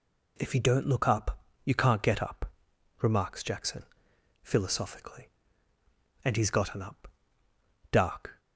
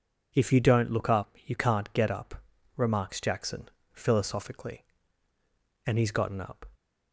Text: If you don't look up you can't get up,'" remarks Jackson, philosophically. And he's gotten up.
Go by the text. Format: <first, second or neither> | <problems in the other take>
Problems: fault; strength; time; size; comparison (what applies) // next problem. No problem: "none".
second | pauses between "up" and "you"; slight; at 1.3 s; 0.26 s long // goes on to say "Dark"; slight; from 7.9 s on; 0.48 s long